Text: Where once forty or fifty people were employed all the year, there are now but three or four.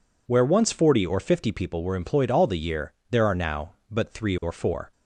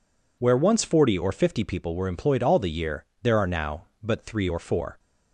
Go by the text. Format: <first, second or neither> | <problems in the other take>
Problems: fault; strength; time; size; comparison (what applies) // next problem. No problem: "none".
neither | none